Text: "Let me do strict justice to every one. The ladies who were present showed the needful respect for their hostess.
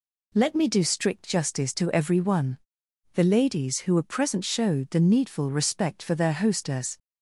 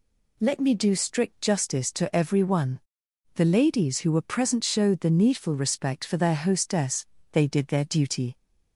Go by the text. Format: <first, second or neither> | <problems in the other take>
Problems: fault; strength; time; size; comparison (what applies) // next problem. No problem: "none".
first | goes on to say "They did their duty"; noticeable; from 7.3 s on; 1.0 s long